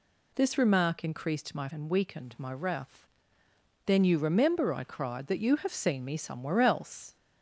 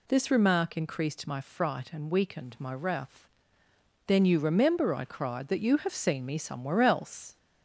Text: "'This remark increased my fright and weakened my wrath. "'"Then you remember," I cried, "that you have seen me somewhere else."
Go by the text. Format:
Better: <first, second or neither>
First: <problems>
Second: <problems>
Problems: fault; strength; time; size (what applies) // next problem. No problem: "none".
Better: second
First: skips "fright"; at 1.6 s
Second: none